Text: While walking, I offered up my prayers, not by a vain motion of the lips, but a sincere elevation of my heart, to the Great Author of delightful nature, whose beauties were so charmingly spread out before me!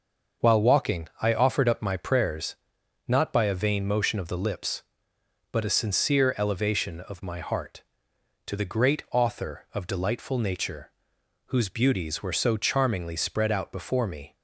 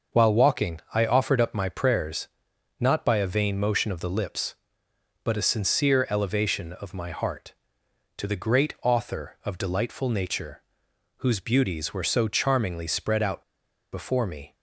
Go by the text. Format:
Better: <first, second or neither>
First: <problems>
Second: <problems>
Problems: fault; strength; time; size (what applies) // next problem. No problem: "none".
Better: first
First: starts louder than the rest; until 1.5 s; 6 dB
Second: starts louder than the rest; until 1.2 s; 6 dB // pauses between "out" and "before"; noticeable; at 13.4 s; 0.48 s long